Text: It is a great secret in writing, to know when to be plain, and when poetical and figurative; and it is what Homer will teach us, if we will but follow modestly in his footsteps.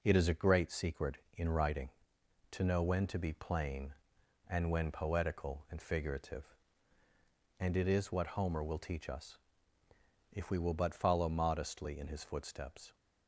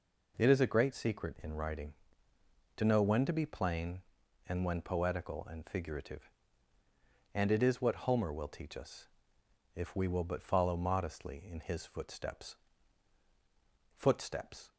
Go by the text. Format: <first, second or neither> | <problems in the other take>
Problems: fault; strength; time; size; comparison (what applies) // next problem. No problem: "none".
first | says "footsteps" twice; at 13.9 s